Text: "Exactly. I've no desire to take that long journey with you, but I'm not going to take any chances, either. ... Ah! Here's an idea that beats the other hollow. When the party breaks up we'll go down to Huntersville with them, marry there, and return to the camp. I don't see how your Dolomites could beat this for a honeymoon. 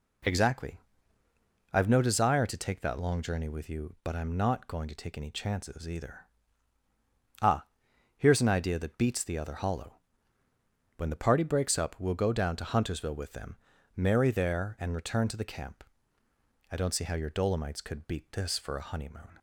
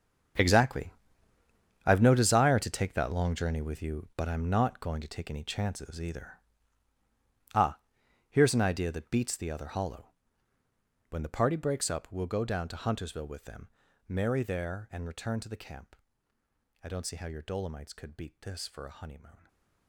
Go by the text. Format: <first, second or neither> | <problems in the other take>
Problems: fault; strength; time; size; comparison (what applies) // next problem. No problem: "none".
first | gets quieter; strong; throughout; 14.5 dB // stays silent after the last word; slight; from 19.3 s on; 0.5 s long